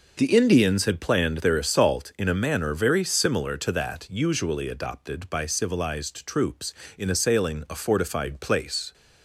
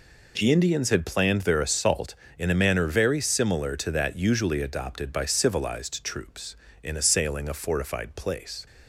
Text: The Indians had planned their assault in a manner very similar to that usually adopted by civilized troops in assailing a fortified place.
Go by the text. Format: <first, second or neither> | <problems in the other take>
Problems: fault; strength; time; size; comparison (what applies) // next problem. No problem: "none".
neither | none